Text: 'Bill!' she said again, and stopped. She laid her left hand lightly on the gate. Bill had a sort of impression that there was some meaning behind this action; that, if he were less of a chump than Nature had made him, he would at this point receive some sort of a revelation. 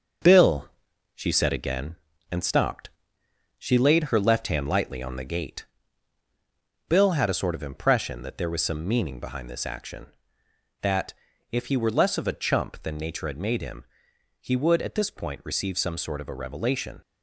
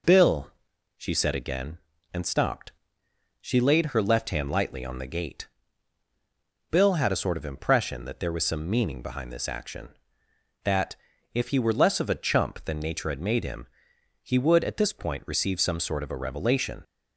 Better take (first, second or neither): second